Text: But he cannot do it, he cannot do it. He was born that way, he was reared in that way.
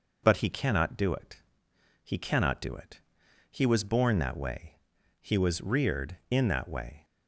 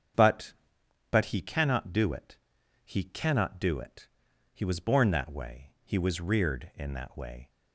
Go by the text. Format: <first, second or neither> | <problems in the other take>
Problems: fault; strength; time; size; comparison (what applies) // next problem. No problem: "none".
first | starts louder than the rest; strong; until 1.7 s; 7.5 dB // says "But" twice; at 1.1 s